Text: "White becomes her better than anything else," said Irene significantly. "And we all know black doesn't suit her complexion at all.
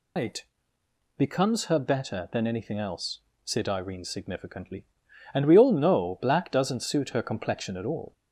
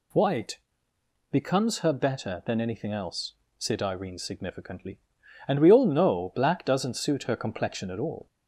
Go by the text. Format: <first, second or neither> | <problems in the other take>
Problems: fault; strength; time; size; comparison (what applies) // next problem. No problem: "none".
second | loses the start of "White"; at 0.1 s; 170 ms // pauses between "White" and "becomes"; noticeable; at 0.4 s; 0.74 s long; noticeable in the second